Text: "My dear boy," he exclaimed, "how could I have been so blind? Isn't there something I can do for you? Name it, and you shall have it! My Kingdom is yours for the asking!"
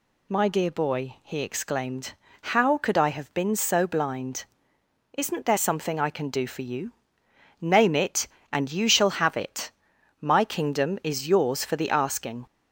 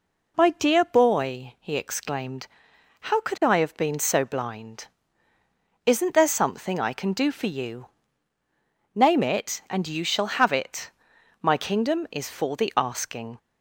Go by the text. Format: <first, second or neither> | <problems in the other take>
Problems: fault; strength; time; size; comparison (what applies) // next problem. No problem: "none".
first | skips "yours"; at 12.2 s